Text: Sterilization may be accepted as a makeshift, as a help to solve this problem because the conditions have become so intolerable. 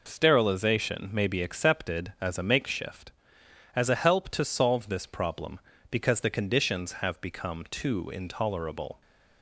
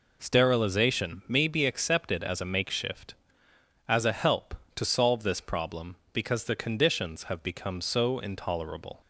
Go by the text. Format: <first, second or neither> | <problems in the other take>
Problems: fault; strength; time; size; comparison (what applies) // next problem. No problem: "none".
second | says "too" for "so"; at 7.7 s